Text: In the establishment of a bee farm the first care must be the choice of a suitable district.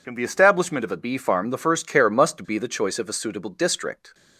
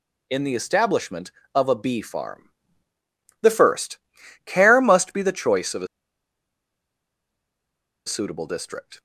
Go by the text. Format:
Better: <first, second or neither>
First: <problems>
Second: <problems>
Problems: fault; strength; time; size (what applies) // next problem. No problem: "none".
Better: first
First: none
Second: pauses between "farm" and "the"; noticeable; at 2.4 s; 0.90 s long // pauses between "first" and "care"; noticeable; at 3.9 s; 0.50 s long // pauses between "a" and "suitable"; strong; at 5.8 s; 2.1 s long